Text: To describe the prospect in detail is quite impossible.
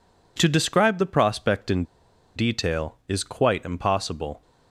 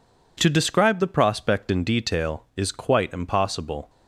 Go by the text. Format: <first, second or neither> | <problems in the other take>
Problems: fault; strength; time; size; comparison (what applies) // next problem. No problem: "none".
second | pauses between "in" and "detail"; noticeable; at 1.8 s; 0.52 s long